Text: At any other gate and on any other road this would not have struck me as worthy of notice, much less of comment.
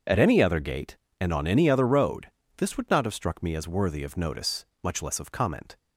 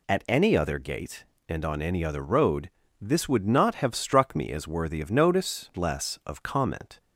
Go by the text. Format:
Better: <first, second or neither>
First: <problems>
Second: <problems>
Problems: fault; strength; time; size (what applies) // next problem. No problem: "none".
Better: first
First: pauses between "road" and "this"; slight; at 2.2 s; 0.32 s long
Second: pauses between "road" and "this"; slight; at 2.6 s; 0.30 s long // skips "much"; at 5.7 s